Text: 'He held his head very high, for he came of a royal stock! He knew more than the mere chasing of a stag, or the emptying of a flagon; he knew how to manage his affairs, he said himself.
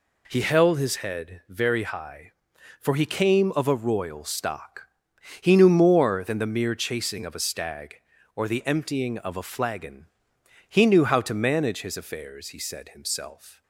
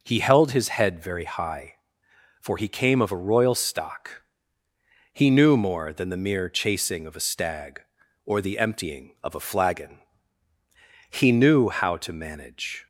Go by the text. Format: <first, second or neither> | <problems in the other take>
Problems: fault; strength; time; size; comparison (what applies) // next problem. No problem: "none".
first | stops before "his affairs he said himself"; at 12.8 s